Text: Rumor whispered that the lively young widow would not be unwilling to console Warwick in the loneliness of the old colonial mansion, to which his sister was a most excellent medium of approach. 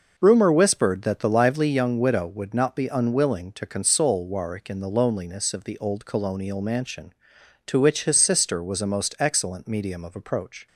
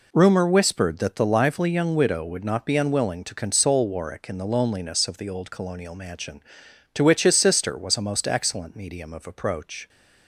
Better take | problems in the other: neither | none

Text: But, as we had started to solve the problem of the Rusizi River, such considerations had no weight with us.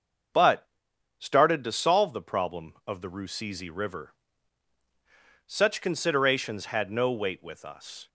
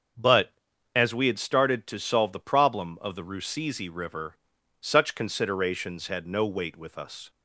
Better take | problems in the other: second | starts louder than the rest; until 1.8 s; 6.5 dB; also in the second // skips "as we had"; at 0.9 s

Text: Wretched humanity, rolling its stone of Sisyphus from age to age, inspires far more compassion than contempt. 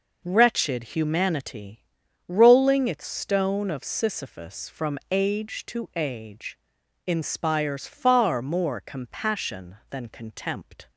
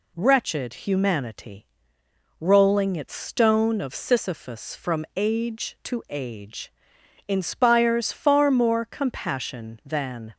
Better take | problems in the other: first | stops before "contempt"; at 10.3 s

